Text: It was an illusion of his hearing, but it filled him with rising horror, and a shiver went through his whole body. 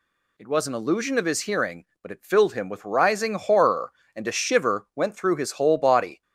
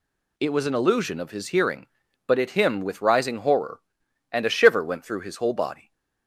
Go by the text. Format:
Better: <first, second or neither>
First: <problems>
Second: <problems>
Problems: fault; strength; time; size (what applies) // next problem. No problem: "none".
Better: first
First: none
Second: skips "filled"; at 2.4 s // stays silent after the last word; slight; from 5.7 s on; 0.5 s long